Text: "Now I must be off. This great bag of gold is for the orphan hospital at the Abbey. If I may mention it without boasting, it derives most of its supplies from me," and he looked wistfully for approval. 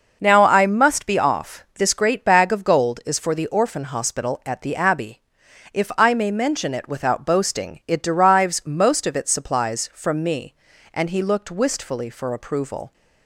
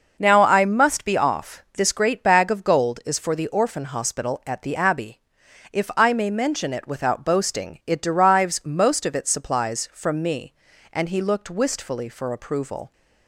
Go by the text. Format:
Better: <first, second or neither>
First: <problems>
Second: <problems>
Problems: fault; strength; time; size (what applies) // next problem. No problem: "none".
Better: neither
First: none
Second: none